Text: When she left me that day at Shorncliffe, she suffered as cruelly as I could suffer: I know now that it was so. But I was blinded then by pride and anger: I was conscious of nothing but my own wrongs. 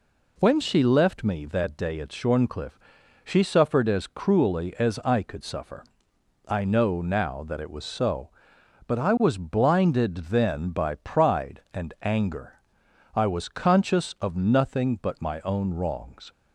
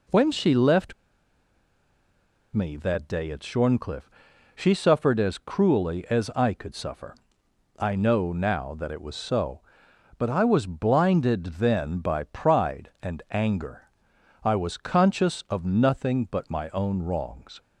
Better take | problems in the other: first | pauses between "left" and "me"; strong; at 0.9 s; 1.6 s long

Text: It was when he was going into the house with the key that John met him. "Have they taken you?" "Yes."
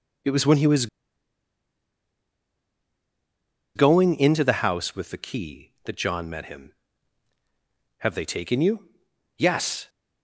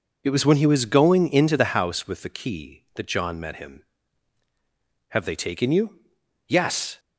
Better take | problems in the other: second | pauses between "was" and "going"; strong; at 0.8 s; 2.8 s long

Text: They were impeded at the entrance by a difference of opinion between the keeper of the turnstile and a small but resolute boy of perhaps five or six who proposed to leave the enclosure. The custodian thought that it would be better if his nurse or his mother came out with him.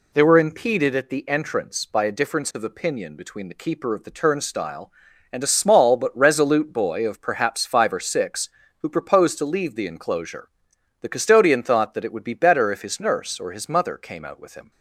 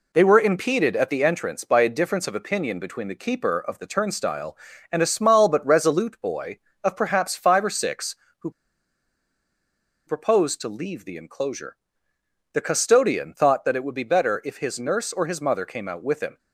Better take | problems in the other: first | pauses between "who" and "proposed"; strong; at 8.5 s; 1.5 s long

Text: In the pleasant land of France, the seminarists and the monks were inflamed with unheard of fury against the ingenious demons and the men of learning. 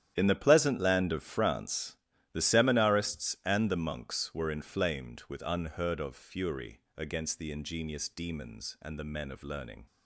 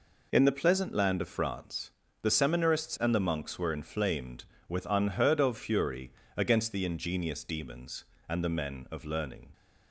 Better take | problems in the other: second | gets quieter; strong; throughout; 14 dB // pauses between "fury" and "against"; slight; at 6.7 s; 0.18 s long; slight in the second

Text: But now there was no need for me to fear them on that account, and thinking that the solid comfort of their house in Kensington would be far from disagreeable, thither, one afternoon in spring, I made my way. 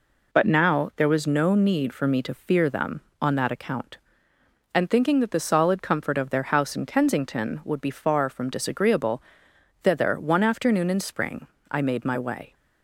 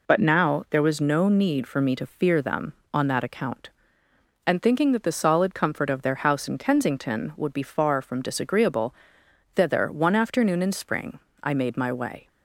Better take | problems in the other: neither | none

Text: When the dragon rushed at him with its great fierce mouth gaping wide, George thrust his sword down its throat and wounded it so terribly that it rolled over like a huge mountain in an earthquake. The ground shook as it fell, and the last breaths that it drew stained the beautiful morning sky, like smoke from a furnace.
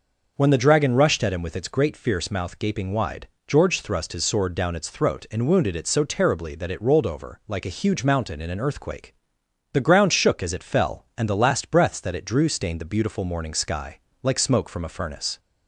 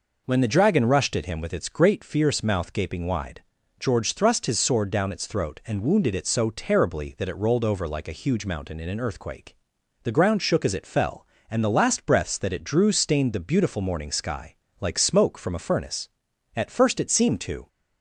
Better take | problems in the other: first | goes on to say "At first it seemed to"; noticeable; from 16.5 s on; 1.1 s long

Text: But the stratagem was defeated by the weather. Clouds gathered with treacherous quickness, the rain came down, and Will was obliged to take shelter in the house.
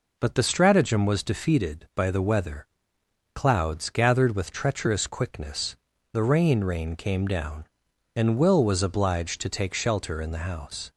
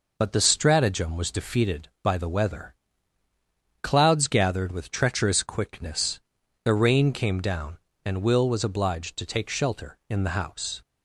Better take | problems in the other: second | says "rain" twice; at 6.6 s

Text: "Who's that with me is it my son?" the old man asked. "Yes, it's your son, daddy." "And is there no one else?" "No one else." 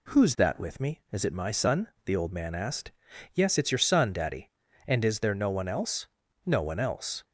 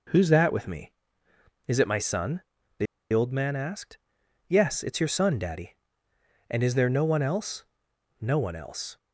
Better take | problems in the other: first | pauses between "the" and "old"; slight; at 2.8 s; 0.27 s long

